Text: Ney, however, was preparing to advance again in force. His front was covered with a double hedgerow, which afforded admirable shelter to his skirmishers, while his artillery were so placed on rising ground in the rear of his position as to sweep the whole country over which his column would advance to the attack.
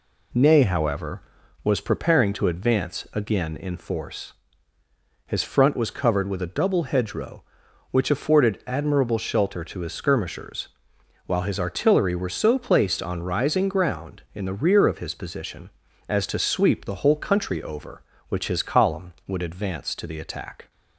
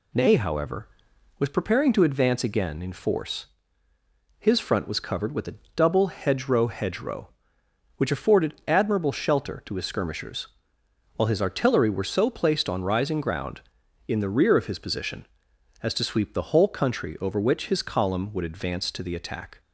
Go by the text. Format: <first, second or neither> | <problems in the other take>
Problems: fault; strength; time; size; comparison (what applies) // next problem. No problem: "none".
first | pauses between "a" and "double"; slight; at 5.5 s; 0.20 s long // says "hedgerow" twice; at 6.6 s